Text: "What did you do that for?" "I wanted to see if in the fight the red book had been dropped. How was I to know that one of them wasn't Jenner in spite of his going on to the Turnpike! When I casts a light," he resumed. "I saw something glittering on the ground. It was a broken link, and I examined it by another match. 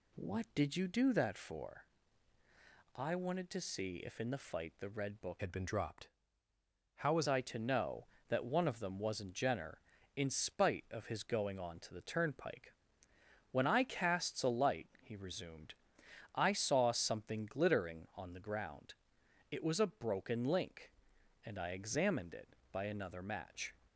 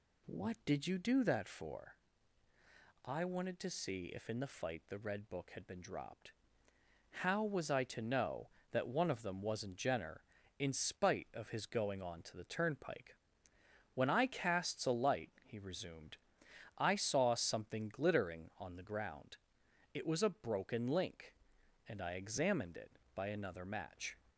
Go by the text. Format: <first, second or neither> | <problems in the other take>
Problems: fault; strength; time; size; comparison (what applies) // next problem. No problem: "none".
second | changes voice from "had" to "was"; from 5.3 to 7.2 s; 1.9 s long